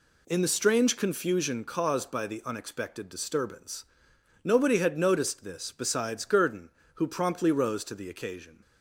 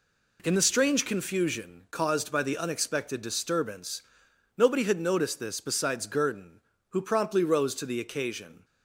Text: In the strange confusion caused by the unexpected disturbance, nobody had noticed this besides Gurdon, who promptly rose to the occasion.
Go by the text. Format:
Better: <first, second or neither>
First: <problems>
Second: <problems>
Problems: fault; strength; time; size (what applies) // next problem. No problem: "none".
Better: neither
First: none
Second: none